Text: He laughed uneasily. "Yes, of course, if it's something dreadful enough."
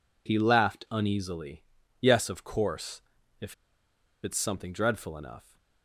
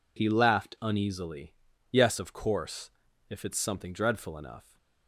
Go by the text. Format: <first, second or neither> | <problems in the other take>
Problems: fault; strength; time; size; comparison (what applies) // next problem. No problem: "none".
second | pauses between "if" and "it's"; noticeable; at 3.5 s; 0.68 s long